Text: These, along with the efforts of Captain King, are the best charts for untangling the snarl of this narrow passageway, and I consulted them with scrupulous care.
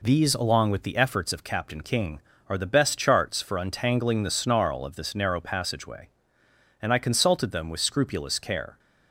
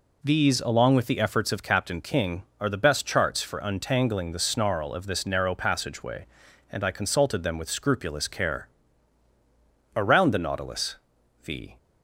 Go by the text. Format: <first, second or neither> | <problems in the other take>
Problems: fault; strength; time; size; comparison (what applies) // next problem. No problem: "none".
first | goes on to say "Around the Nautilus the"; strong; from 9.9 s on; 1.8 s long